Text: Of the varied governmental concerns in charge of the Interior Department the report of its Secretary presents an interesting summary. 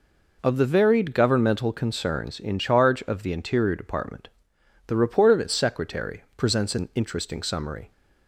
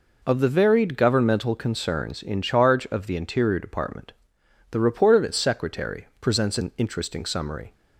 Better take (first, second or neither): neither